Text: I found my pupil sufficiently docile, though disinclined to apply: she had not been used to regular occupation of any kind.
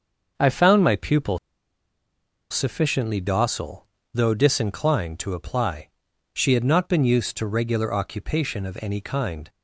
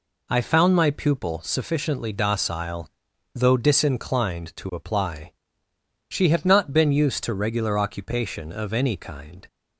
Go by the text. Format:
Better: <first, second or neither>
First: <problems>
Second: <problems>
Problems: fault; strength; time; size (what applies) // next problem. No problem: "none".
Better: second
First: starts louder than the rest; until 1.3 s; 6 dB // pauses between "pupil" and "sufficiently"; at 1.3 s; 1.1 s long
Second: none